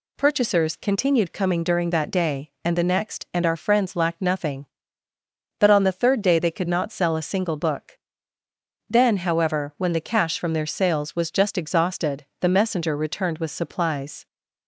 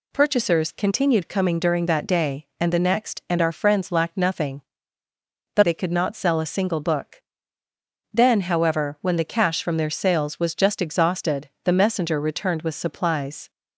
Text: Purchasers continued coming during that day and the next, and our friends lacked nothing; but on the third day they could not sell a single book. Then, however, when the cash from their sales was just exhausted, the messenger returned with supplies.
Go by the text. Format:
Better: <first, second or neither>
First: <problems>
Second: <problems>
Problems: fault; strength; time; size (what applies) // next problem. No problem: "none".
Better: first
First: none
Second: skips "on the third day"; at 5.6 s